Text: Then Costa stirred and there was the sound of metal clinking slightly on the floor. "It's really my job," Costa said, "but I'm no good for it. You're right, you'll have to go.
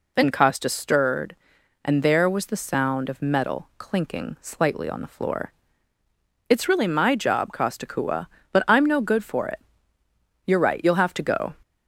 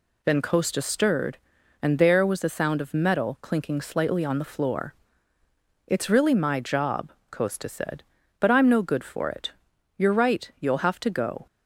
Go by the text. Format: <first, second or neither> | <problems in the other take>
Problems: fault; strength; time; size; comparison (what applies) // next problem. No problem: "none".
second | says "kua" for "said"; at 7.8 s